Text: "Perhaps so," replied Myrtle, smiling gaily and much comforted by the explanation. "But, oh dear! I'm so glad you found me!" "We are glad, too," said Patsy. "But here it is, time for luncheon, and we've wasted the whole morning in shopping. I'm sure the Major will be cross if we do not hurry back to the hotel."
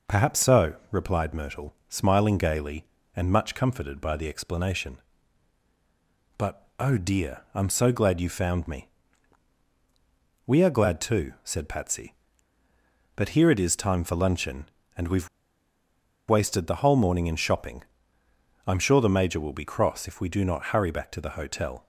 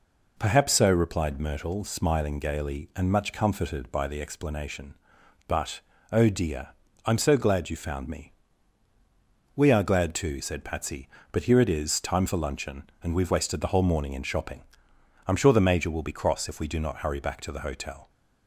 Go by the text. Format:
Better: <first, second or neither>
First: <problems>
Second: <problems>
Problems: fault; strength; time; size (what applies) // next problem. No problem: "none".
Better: second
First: pauses between "we've" and "wasted"; at 15.2 s; 1.0 s long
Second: none